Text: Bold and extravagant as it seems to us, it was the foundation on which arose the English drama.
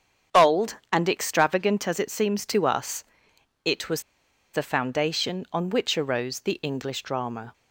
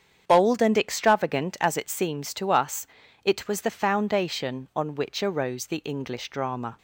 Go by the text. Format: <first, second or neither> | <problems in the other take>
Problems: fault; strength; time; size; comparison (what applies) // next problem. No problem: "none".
second | starts louder than the rest; strong; until 1.4 s; 8 dB; strong in the second // pauses between "was" and "the"; noticeable; at 4.0 s; 0.51 s long